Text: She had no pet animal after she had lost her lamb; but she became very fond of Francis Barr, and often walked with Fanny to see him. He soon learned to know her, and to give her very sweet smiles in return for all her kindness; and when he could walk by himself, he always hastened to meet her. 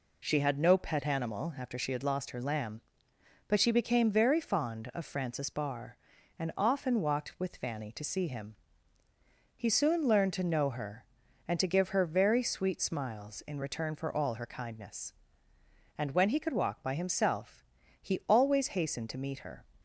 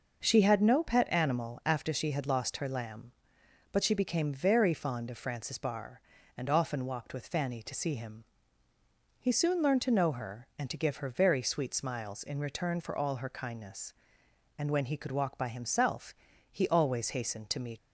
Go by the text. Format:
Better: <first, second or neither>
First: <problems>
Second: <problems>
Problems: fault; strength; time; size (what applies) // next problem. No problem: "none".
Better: first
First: none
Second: stops before "her"; at 17.7 s